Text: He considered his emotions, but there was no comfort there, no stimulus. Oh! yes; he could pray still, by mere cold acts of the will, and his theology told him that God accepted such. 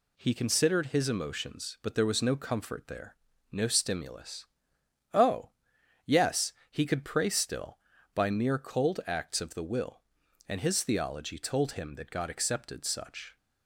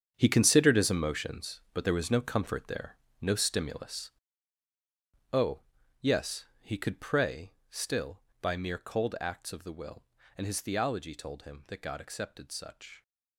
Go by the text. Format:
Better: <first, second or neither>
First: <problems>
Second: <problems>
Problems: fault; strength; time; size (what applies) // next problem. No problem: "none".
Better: first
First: none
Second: gets quieter; strong; throughout; 13.5 dB // pauses between "pray" and "still"; slight; at 7.5 s; 0.16 s long